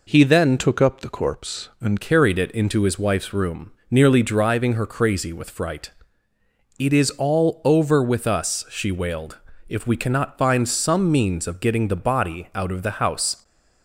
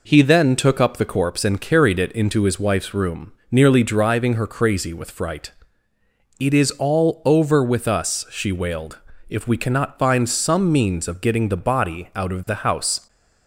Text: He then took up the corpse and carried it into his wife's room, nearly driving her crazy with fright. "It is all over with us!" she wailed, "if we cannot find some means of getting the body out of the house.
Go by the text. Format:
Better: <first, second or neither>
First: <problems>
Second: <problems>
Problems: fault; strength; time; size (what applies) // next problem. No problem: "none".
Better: second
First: changes voice from "took" to "and"; from 0.5 to 2.0 s; 1.5 s long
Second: none